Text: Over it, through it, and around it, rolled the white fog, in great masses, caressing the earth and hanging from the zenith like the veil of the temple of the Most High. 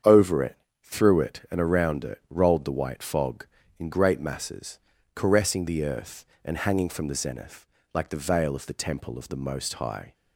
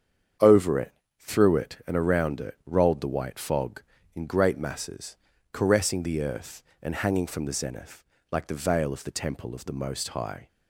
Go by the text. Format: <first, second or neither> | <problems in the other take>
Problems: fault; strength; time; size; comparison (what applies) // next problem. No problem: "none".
neither | starts louder than the rest; strong; the same in both // pauses between "zenith" and "like"; slight; the same in both